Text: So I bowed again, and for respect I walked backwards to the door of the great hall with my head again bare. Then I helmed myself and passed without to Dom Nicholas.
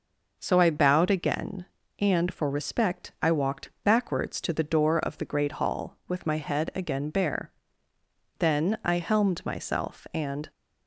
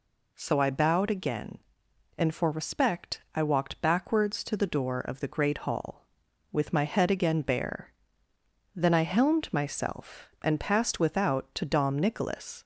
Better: second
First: stops before "passed without to Dom Nicholas"; at 10.5 s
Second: none

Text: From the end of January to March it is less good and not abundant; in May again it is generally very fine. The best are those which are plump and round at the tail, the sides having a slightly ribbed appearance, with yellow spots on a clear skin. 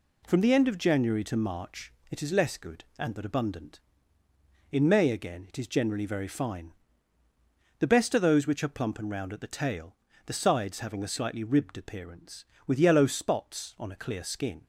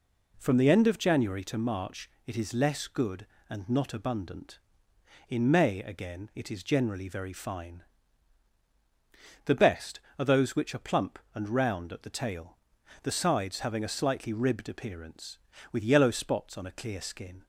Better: second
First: pauses between "March" and "it"; slight; at 1.9 s; 0.18 s long // says "but" for "not"; at 3.1 s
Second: pauses between "March" and "it"; slight; at 2.0 s; 0.18 s long

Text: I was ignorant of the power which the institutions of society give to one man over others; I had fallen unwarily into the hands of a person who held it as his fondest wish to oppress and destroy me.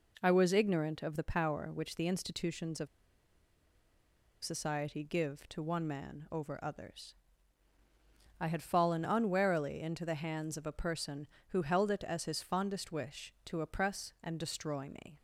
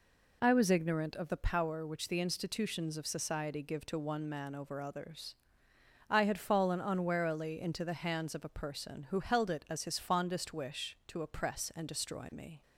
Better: second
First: pauses between "of" and "society"; strong; at 2.8 s; 1.5 s long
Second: none

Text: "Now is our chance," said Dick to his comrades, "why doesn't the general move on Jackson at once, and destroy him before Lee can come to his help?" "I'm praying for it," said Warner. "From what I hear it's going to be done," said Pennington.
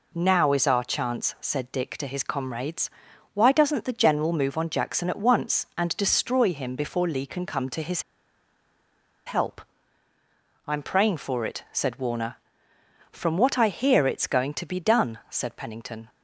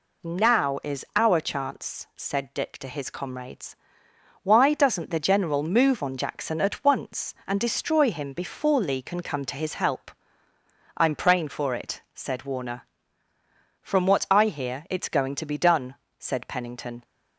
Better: second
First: pauses between "his" and "help"; at 8.0 s; 1.2 s long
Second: none

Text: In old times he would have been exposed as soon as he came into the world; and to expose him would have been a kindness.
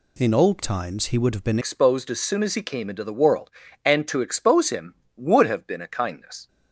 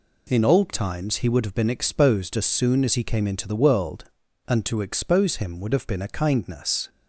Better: second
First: changes voice at "exposed"; from 1.6 s on; 4.8 s long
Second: none

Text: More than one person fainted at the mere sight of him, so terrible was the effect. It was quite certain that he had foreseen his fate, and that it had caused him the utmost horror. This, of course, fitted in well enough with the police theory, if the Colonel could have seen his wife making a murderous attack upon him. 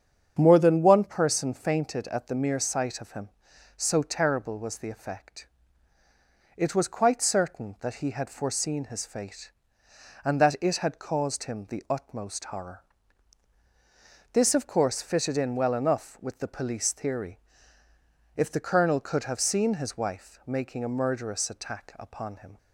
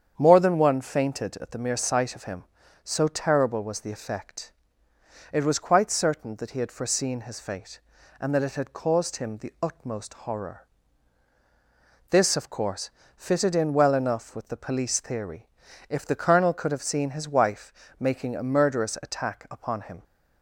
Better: first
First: starts louder than the rest; strong; until 1.4 s; 7.5 dB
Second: starts louder than the rest; strong; until 1.1 s; 8 dB // skips "person"; at 0.7 s // pauses between "wife" and "making"; slight; at 17.7 s; 0.26 s long

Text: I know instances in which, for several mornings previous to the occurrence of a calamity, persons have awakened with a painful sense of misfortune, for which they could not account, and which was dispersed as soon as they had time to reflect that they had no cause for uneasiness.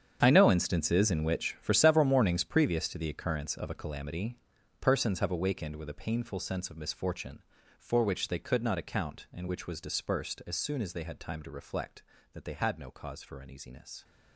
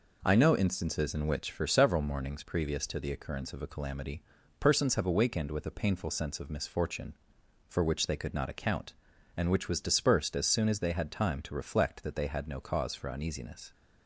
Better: second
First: gets quieter; strong; throughout; 14.5 dB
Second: none

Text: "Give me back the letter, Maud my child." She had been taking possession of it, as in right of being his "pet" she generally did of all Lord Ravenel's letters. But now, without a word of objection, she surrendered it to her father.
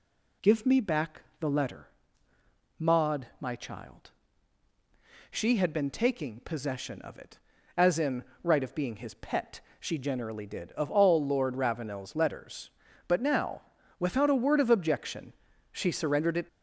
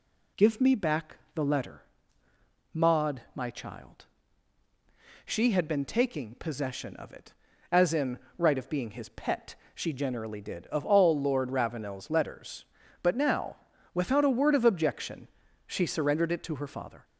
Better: second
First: pauses between "back" and "the"; slight; at 1.2 s; 0.16 s long // pauses between "in" and "right"; slight; at 8.2 s; 0.20 s long // pauses between "pet" and "she"; slight; at 9.5 s; 0.20 s long // stops before "to her father"; at 16.4 s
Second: pauses between "back" and "the"; slight; at 1.1 s; 0.16 s long // pauses between "in" and "right"; slight; at 8.1 s; 0.20 s long // pauses between "pet" and "she"; slight; at 9.5 s; 0.20 s long

